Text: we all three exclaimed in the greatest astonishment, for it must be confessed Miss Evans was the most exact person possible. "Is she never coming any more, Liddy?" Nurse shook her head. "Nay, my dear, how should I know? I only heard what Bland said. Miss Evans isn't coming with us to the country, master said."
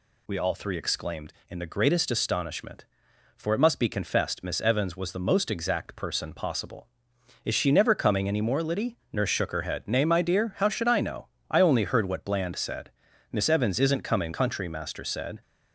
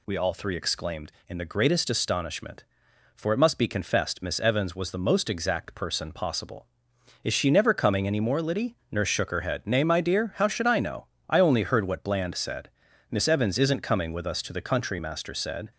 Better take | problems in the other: second | skips "with us to the"; at 14.3 s

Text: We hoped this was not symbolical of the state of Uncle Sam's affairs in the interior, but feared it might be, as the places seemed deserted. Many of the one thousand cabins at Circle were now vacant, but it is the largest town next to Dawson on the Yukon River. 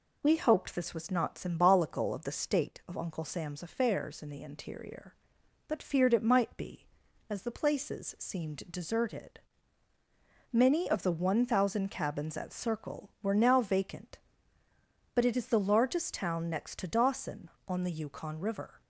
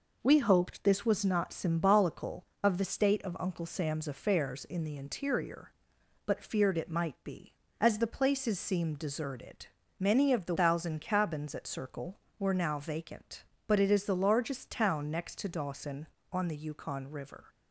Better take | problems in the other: first | skips "one"; at 10.5 s

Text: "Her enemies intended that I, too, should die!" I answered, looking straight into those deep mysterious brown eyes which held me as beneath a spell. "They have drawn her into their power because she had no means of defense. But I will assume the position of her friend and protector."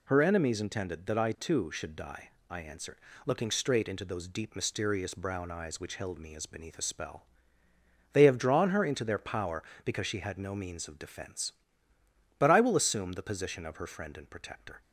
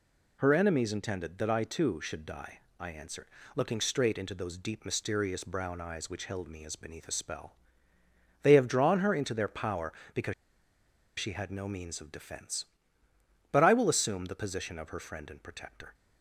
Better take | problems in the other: first | pauses between "because" and "she"; noticeable; at 10.3 s; 0.85 s long

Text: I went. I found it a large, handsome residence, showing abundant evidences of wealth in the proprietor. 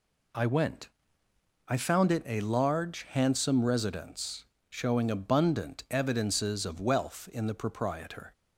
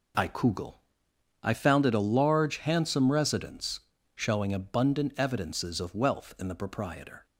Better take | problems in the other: first | says "kugel" for "went"; at 0.2 s

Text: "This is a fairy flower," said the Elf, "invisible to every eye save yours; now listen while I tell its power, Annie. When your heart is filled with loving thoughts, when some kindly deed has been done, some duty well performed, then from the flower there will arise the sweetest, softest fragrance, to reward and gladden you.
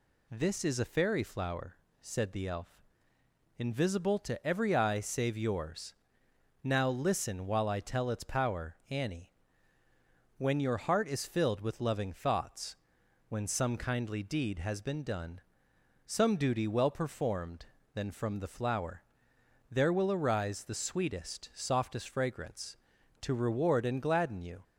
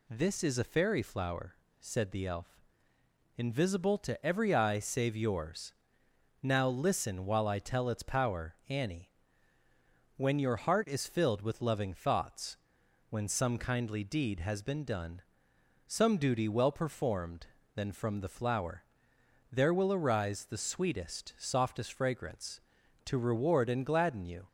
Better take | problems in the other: neither | pauses between "flower" and "there"; noticeable; the same in both

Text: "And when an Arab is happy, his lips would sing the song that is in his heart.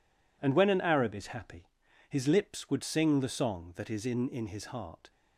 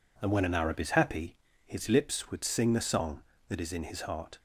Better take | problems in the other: second | says "in" twice; at 4.2 s

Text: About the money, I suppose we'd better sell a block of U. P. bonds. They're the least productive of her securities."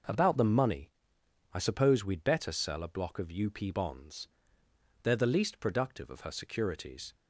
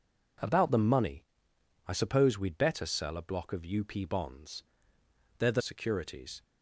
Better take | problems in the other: first | skips "least productive of her"; at 5.6 s

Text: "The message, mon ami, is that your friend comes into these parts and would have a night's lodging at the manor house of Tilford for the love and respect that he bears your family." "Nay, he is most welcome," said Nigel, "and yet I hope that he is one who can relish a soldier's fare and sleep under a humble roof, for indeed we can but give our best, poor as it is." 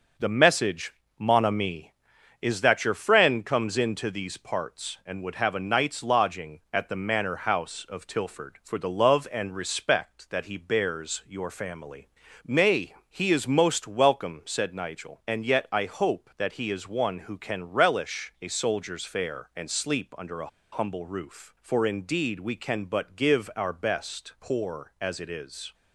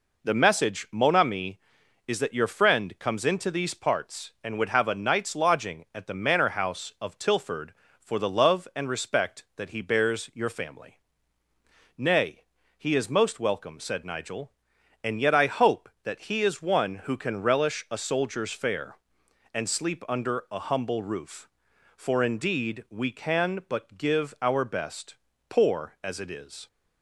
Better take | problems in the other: second | pauses between "a" and "humble"; slight; at 20.4 s; 0.23 s long

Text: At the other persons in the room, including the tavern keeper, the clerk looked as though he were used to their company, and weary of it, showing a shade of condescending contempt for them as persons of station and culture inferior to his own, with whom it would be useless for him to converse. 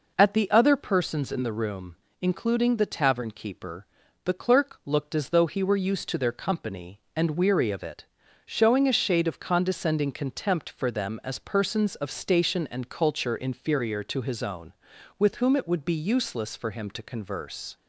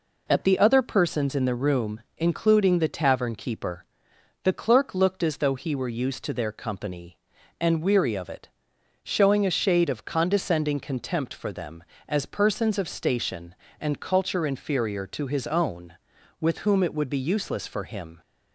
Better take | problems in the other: first | stops before "to converse"; at 18.2 s

